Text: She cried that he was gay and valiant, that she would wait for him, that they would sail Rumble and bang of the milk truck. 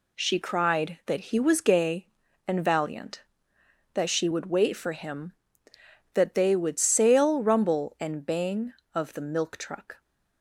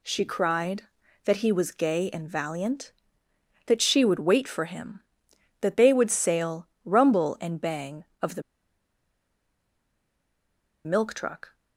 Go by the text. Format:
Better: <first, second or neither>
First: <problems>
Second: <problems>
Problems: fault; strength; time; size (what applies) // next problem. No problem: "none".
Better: first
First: none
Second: pauses between "sail" and "Rumble"; slight; at 6.6 s; 0.16 s long // pauses between "the" and "milk"; strong; at 8.4 s; 2.4 s long